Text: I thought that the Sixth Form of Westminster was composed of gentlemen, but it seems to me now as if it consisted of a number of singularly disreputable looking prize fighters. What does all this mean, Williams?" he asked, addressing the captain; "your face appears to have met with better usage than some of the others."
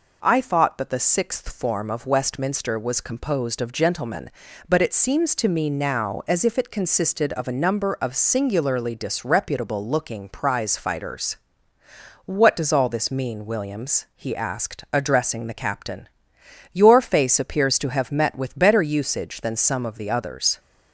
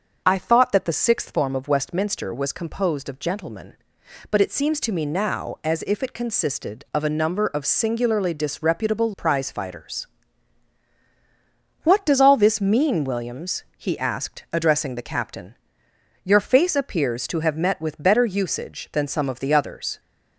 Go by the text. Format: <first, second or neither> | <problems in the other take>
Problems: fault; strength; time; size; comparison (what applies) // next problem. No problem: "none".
first | starts louder than the rest; until 1.2 s; 6.5 dB // skips "looking"; at 9.1 s